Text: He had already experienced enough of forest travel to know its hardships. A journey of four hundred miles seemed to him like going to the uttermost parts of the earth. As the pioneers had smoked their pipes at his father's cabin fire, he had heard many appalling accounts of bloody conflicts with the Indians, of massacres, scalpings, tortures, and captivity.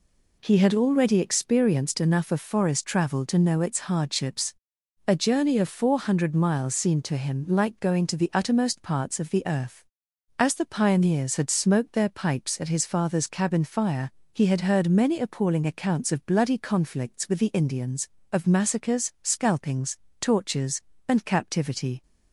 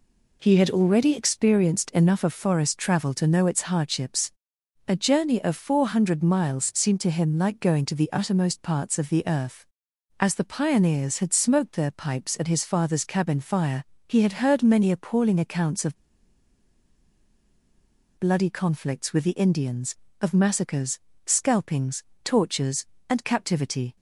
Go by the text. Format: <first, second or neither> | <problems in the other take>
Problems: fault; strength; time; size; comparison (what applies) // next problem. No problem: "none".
first | pauses between "of" and "bloody"; strong; at 15.9 s; 2.2 s long